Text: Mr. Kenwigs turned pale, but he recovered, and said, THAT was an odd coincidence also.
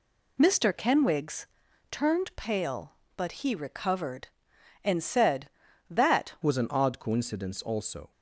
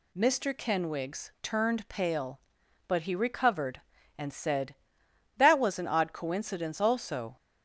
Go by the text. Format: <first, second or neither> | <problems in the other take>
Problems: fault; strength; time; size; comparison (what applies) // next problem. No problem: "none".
second | pauses between "Kenwigs" and "turned"; at 1.4 s; 0.44 s long // changes voice at "was"; from 6.4 s on; 1.7 s long